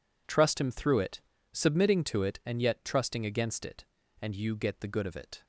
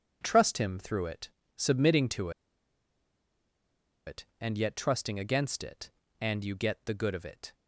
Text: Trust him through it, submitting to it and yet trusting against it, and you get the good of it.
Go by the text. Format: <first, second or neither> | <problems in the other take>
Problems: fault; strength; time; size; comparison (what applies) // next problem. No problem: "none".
first | pauses between "to" and "it"; strong; at 2.3 s; 1.7 s long